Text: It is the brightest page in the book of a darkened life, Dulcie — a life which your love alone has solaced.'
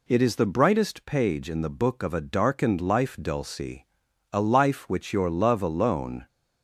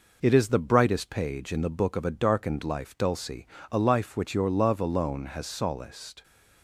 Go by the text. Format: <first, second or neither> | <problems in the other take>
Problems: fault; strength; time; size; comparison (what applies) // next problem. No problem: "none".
second | stops before "has solaced"; at 6.2 s